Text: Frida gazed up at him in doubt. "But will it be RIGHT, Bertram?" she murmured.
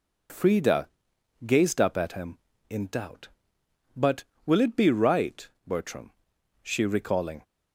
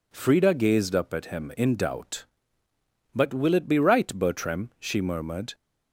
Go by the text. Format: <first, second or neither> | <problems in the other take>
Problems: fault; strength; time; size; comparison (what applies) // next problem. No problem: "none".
second | pauses between "Frida" and "gazed"; noticeable; at 0.8 s; 0.58 s long // says "recalling" for "murmured"; at 6.8 s